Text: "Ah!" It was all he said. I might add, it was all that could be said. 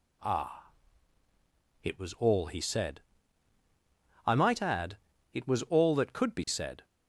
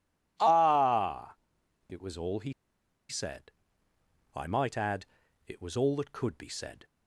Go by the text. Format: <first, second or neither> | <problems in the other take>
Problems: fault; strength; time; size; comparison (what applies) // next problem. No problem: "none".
first | pauses between "he" and "said"; noticeable; at 2.5 s; 0.56 s long